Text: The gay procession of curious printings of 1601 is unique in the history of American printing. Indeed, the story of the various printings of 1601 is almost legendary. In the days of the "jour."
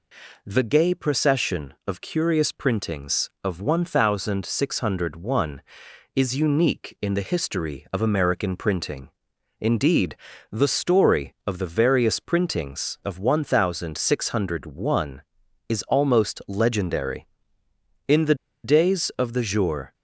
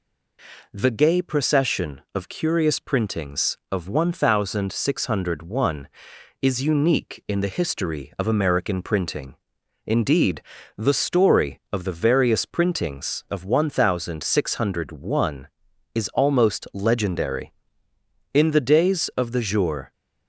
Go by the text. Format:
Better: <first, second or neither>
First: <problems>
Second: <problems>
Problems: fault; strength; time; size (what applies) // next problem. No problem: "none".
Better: second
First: pauses between "the" and "days"; slight; at 18.3 s; 0.29 s long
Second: none